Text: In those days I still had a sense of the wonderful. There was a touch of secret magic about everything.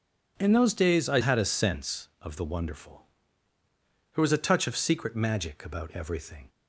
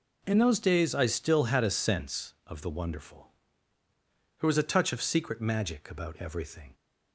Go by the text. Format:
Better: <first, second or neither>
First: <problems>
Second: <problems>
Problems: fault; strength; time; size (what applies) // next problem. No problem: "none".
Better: second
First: skips "still"; at 1.2 s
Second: none